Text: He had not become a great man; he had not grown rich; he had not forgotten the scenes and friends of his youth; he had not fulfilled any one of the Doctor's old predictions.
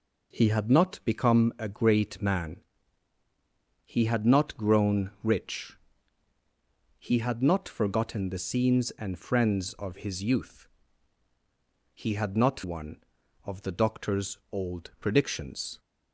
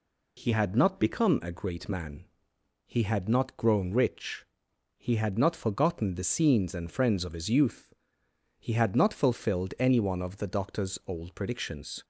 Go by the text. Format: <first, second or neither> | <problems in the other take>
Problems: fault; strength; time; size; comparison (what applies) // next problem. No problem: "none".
second | skips "fulfilled any"; at 12.6 s